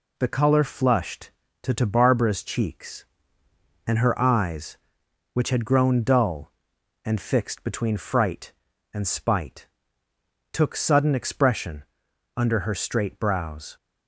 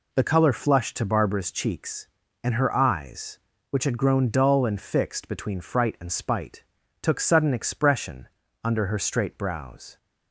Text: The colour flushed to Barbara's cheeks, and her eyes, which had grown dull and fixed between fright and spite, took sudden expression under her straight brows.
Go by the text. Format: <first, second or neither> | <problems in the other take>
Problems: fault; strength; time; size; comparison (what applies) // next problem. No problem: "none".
second | says "to" twice; at 1.7 s // pauses between "expression" and "under"; noticeable; at 11.8 s; 0.50 s long; slight in the second